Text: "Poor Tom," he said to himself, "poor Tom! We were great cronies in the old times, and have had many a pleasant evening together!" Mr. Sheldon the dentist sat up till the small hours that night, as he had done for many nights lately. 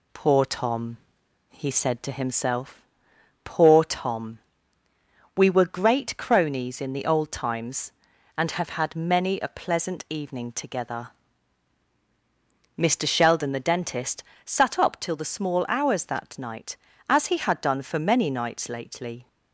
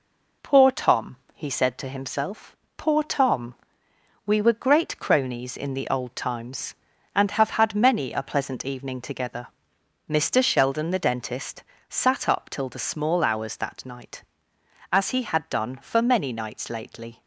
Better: first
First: pauses between "dentist" and "sat"; slight; at 14.2 s; 0.20 s long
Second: gets quieter; slight; throughout; 2.5 dB // pauses between "dentist" and "sat"; slight; at 11.6 s; 0.26 s long

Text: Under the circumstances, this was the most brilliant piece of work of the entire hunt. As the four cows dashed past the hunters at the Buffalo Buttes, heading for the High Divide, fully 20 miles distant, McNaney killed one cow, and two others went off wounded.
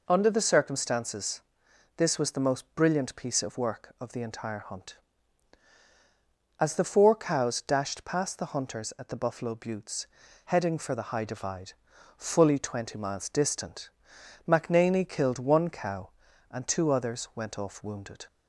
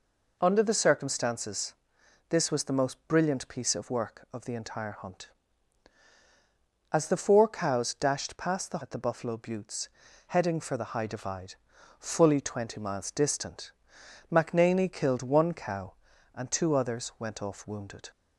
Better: first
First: none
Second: skips "hunters"; at 8.8 s

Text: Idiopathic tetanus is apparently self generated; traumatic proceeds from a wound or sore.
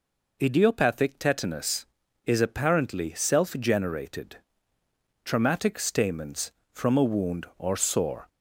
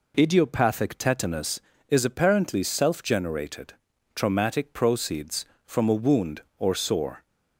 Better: second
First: says "stamens" for "proceeds"; at 5.7 s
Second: none

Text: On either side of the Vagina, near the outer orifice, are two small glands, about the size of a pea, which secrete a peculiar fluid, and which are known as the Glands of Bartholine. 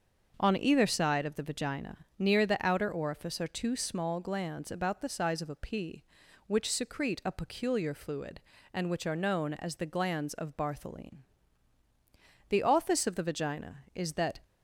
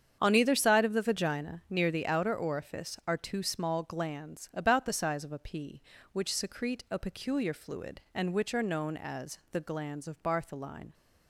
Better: second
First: starts louder than the rest; until 1.3 s; 6.5 dB // goes on to say "The office of the Vagina is that"; strong; from 12.4 s on; 1.9 s long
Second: starts louder than the rest; strong; until 1.2 s; 8 dB

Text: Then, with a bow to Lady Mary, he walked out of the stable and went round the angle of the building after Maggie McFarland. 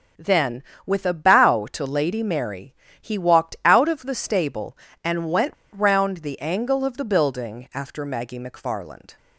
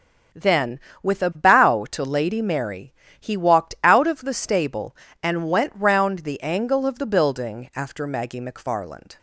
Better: second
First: starts louder than the rest; until 1.3 s; 6.5 dB // pauses between "went" and "round"; slight; at 5.5 s; 0.21 s long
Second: starts louder than the rest; strong; until 1.6 s; 7.5 dB

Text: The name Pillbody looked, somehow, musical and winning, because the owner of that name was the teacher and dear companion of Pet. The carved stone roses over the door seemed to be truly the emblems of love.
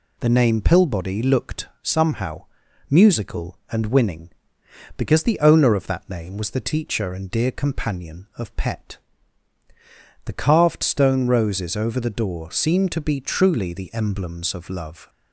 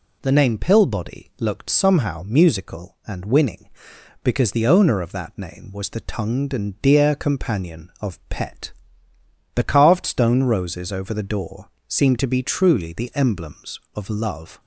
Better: first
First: none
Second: says "tongued" for "teacher"; at 6.0 s // pauses between "door" and "seemed"; slight; at 11.6 s; 0.18 s long

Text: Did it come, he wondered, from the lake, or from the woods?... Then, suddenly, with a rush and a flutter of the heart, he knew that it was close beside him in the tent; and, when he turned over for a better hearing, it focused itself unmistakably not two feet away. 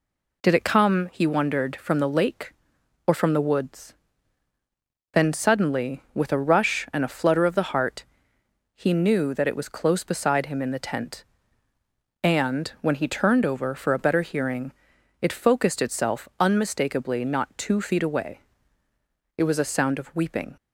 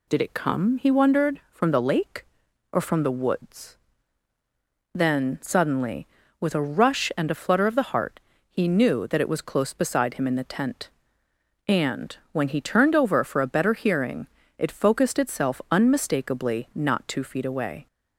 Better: second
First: goes on to say "It was a sound of weeping"; noticeable; from 19.3 s on; 1.2 s long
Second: none

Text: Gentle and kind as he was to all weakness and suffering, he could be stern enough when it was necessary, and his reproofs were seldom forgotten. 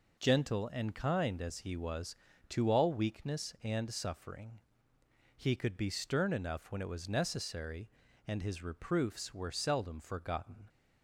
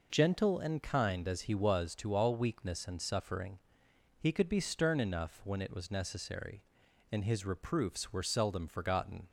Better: neither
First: none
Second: none

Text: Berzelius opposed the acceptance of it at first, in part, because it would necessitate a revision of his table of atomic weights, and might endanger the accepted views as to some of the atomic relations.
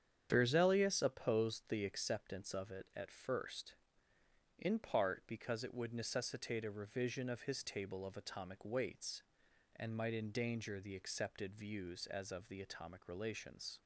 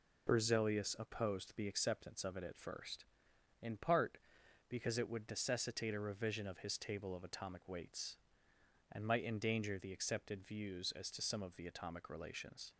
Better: second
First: starts louder than the rest; strong; until 1.3 s; 8.5 dB // skips "to some"; at 12.3 s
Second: none

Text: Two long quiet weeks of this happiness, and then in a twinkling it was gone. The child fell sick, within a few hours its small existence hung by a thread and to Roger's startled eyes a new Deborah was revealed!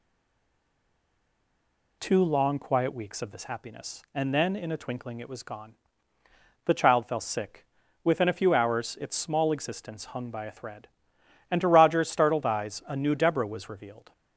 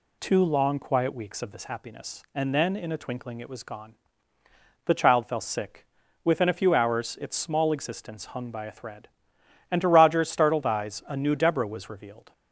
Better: second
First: stays silent before the first word; noticeable; until 1.9 s; 1.9 s long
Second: none

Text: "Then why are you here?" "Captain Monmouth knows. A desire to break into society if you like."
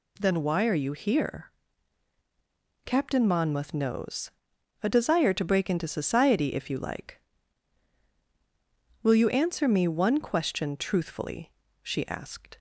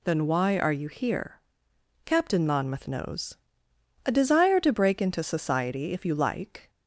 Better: second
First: goes on to say "Will you answer me one question truthfully she asked"; strong; from 9.0 s on; 3.5 s long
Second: none

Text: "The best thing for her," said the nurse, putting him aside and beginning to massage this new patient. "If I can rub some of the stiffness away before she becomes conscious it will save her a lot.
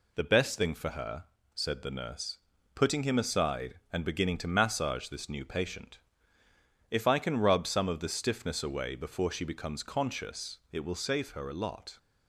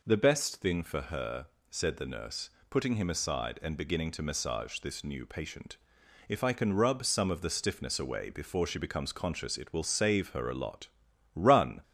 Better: first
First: none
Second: goes on to say "Run"; slight; from 11.3 s on; 0.46 s long

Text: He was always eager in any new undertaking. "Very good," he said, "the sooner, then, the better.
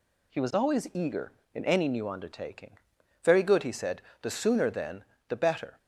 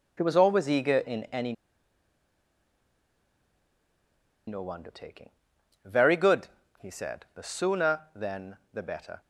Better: first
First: none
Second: pauses between "any" and "new"; strong; at 1.5 s; 2.9 s long

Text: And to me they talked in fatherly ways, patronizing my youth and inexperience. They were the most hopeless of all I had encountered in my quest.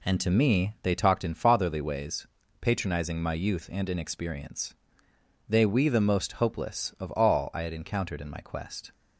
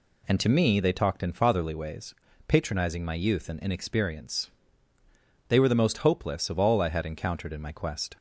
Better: second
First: says "we" for "were"; at 5.6 s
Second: none

